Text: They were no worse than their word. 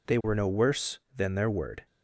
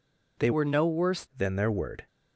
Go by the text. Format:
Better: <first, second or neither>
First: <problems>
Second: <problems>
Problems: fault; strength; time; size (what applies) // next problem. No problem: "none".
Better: first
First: none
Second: changes voice from "were" to "worse"; from 0.5 to 1.2 s; 0.7 s long